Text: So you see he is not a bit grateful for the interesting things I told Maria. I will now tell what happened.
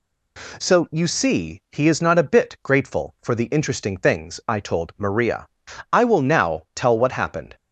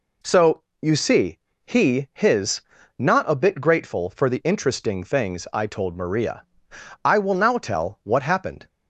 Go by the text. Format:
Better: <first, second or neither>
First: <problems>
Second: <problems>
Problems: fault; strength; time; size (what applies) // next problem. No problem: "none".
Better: first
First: none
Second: pauses between "So" and "you"; slight; at 0.6 s; 0.22 s long // pauses between "see" and "he"; slight; at 1.3 s; 0.26 s long // says "his" for "is"; at 2.1 s